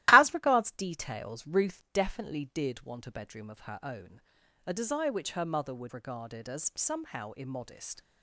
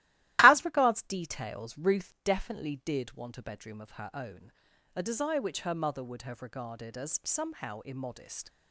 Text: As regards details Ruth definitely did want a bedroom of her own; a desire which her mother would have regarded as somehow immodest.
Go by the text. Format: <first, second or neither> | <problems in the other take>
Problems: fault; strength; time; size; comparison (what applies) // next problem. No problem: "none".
second | starts louder than the rest; strong; until 1.1 s; 15.5 dB; strong in the second // skips "have"; at 5.9 s